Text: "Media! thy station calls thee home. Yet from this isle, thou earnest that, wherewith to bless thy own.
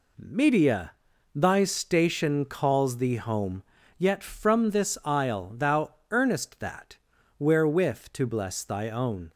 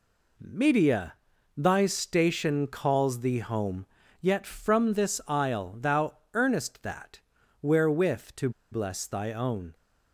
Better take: first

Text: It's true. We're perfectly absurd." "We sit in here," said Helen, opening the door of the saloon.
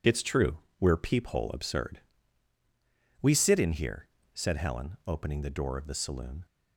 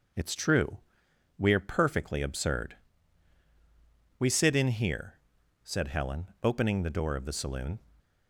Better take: second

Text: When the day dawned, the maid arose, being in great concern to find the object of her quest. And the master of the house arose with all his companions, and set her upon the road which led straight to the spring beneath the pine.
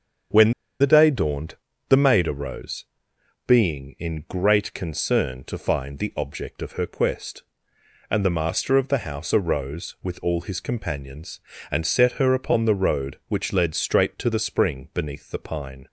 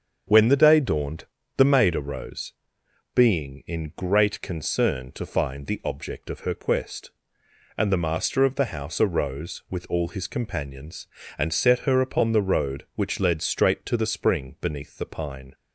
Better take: second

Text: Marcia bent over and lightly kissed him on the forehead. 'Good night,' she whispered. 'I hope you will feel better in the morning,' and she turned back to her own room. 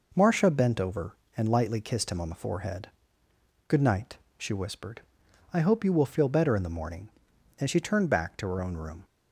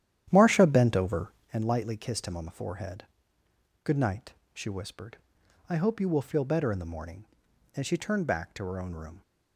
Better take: first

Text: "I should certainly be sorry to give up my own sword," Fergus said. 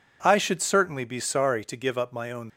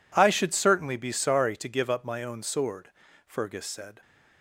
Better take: second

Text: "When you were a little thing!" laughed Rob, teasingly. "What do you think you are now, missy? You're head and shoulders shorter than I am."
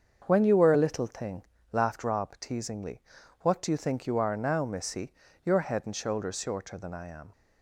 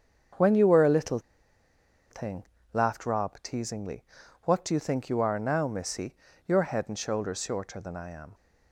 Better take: first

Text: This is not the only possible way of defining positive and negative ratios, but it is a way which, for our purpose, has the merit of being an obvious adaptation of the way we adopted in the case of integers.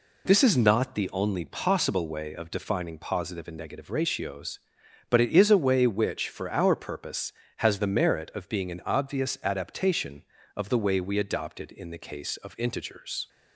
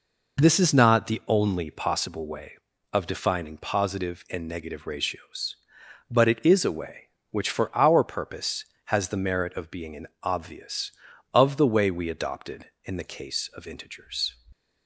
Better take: first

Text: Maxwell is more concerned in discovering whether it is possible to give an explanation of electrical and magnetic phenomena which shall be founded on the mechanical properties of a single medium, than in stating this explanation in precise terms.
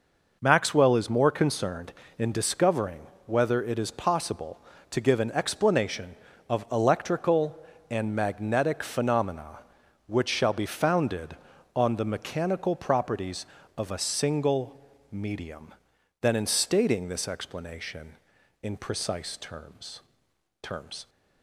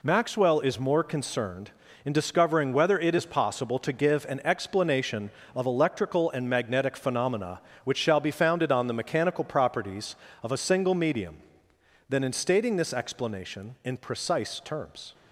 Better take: second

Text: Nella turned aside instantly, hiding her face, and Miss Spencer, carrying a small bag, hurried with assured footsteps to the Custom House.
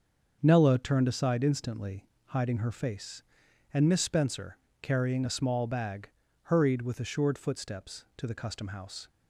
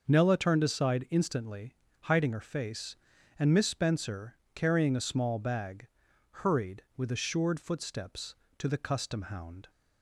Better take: first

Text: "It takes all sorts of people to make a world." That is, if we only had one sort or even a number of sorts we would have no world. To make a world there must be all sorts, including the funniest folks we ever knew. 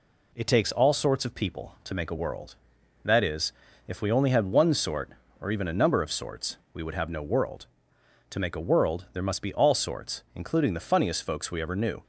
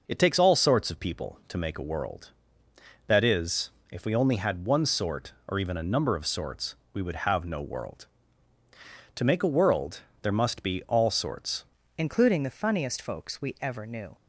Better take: first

